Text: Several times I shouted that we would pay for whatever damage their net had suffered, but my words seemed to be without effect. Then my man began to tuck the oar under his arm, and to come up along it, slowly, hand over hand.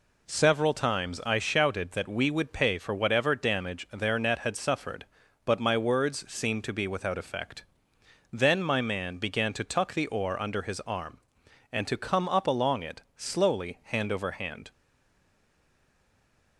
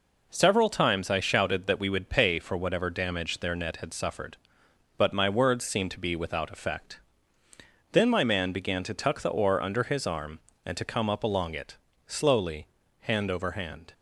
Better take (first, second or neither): second